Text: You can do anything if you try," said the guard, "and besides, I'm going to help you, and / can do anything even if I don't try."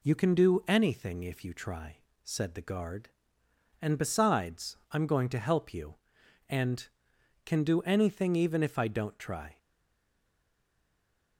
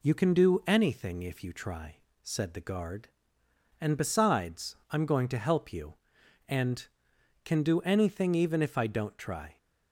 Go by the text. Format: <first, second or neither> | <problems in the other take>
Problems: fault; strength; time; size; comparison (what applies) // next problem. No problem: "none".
second | stays silent after the last word; noticeable; from 9.5 s on; 1.8 s long